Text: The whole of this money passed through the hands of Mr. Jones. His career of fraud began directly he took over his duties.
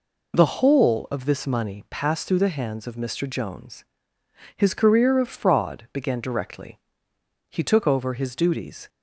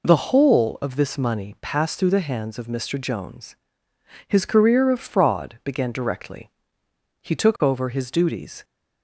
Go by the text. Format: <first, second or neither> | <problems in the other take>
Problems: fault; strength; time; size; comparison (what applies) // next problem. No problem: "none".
neither | pauses between "directly" and "he"; noticeable; the same in both